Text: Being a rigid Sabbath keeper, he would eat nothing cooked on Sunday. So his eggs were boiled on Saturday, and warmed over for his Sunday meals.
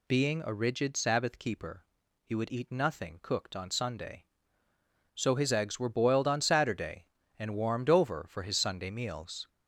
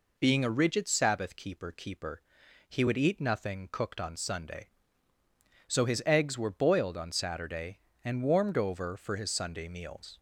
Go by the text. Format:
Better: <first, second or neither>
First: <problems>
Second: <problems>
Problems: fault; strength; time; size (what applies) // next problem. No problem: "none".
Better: first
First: none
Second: says "keeper" twice; at 1.7 s